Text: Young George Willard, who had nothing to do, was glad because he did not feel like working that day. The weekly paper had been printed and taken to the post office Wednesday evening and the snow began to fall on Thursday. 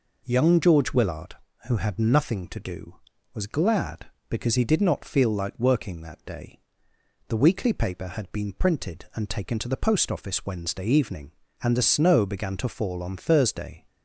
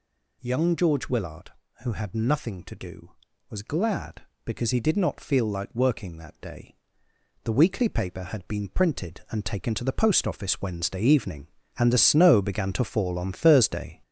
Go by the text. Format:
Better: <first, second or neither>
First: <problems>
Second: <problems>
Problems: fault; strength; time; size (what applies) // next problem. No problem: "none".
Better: first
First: none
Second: gets louder; noticeable; throughout; 5 dB